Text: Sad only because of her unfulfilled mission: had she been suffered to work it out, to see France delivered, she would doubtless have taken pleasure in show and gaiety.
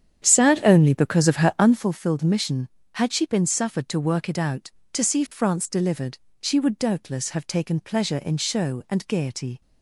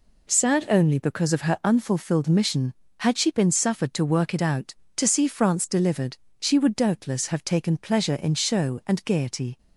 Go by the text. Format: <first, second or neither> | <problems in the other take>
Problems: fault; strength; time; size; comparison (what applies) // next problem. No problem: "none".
second | starts louder than the rest; strong; until 1.9 s; 9 dB